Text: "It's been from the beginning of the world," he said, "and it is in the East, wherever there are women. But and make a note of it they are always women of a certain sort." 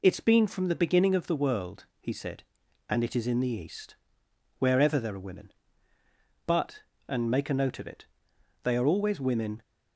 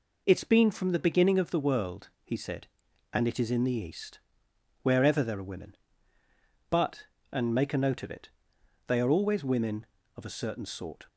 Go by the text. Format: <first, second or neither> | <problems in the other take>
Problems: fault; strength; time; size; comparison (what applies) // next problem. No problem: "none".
second | pauses between "it" and "they"; noticeable; at 8.0 s; 0.56 s long; noticeable in the second // stops before "of a certain sort"; at 9.6 s